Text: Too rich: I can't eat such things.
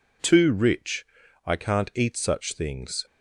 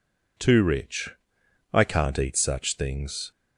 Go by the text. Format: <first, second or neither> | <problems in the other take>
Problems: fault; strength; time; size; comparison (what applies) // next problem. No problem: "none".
neither | none